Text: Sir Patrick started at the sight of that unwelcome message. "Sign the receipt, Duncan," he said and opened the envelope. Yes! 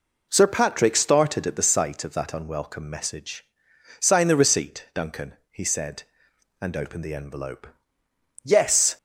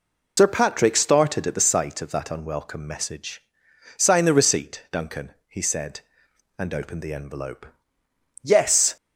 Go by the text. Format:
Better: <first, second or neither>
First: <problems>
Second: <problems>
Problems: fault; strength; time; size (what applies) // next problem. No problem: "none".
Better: first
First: none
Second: loses the start of "Sir"; at 0.3 s; 65 ms